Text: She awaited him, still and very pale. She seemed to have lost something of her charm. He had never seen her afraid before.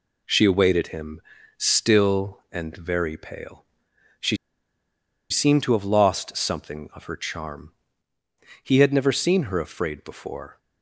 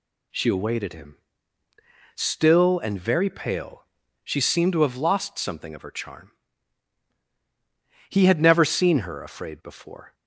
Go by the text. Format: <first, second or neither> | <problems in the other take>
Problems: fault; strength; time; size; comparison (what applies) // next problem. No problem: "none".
second | pauses between "She" and "seemed"; noticeable; at 4.3 s; 0.94 s long